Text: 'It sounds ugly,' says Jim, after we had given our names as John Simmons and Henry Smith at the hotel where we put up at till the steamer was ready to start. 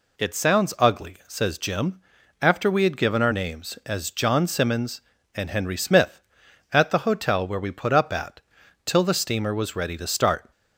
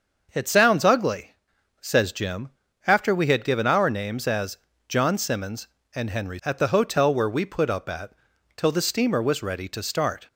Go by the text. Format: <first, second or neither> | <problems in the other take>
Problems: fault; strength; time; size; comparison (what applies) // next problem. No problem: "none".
first | starts louder than the rest; until 1.3 s; 6.5 dB // pauses between "as" and "John"; slight; at 4.5 s; 0.30 s long // skips "Smith"; at 6.4 s // pauses between "at" and "till"; at 8.1 s; 0.44 s long; also in the first